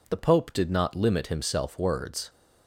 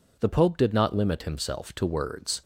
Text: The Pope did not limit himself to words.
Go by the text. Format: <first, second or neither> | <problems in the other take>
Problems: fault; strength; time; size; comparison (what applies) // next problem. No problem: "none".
second | skips "to"; at 1.7 s